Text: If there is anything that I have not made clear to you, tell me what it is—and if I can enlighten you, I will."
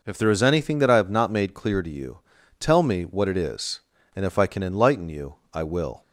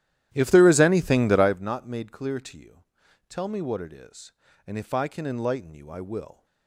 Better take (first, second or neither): first